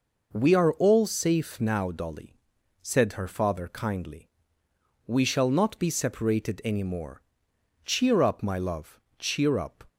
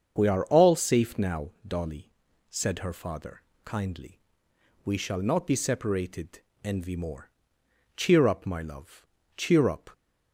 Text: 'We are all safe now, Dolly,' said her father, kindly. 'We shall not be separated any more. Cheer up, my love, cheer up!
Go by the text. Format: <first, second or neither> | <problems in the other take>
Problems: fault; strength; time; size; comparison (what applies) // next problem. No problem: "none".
first | starts louder than the rest; until 1.1 s; 7 dB // says "envy" for "any"; at 6.6 s